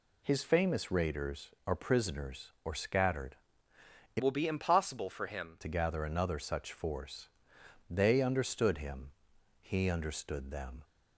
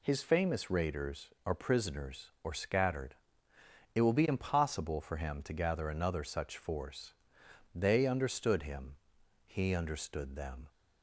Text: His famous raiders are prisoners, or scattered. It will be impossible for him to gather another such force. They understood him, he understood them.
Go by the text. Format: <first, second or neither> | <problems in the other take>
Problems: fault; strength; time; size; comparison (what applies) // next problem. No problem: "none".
second | changes voice from "will" to "him"; from 4.2 to 5.5 s; 1.3 s long